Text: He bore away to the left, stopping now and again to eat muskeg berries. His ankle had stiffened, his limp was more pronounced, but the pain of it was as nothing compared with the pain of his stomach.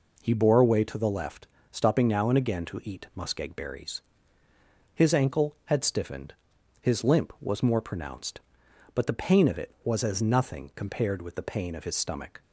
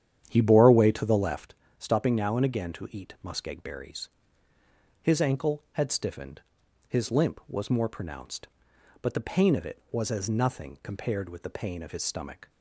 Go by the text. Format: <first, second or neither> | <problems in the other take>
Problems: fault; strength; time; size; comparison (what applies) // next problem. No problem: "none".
first | starts louder than the rest; strong; until 1.5 s; 9.5 dB